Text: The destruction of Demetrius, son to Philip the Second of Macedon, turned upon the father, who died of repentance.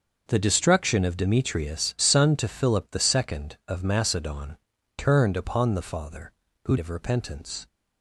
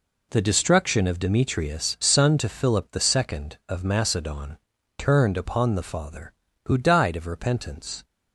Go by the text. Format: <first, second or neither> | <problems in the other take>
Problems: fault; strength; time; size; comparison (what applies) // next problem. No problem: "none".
second | starts louder than the rest; until 1.2 s; 6 dB // skips "died"; at 6.7 s